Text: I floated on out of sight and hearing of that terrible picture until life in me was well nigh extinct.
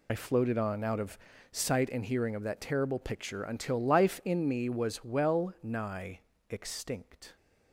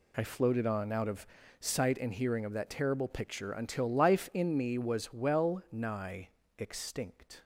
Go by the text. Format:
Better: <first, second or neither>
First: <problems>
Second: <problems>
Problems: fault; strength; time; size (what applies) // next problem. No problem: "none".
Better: second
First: loses the start of "I"; at 0.0 s; 40 ms // pauses between "of" and "sight"; slight; at 1.1 s; 0.34 s long // pauses between "nigh" and "extinct"; slight; at 6.1 s; 0.30 s long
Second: pauses between "of" and "sight"; slight; at 1.2 s; 0.34 s long // pauses between "nigh" and "extinct"; slight; at 6.2 s; 0.29 s long